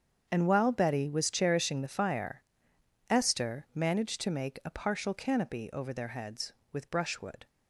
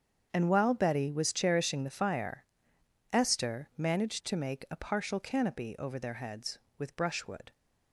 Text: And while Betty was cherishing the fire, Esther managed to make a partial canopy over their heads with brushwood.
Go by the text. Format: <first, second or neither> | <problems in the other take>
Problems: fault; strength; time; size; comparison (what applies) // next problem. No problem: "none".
neither | starts louder than the rest; strong; the same in both